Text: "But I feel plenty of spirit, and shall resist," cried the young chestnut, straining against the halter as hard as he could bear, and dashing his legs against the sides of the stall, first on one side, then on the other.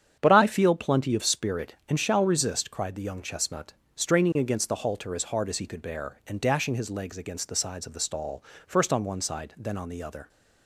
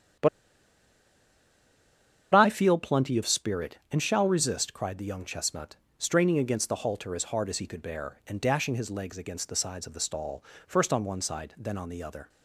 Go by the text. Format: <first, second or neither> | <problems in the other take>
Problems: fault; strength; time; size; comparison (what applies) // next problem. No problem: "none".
first | starts louder than the rest; strong; until 3.2 s; 8 dB; strong in the first // pauses between "But" and "I"; strong; at 0.2 s; 2.0 s long